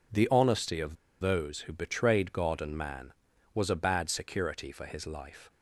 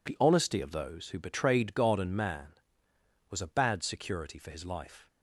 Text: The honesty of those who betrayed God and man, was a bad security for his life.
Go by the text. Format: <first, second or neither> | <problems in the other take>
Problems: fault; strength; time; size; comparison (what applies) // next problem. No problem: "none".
second | pauses between "of" and "those"; slight; at 0.9 s; 0.25 s long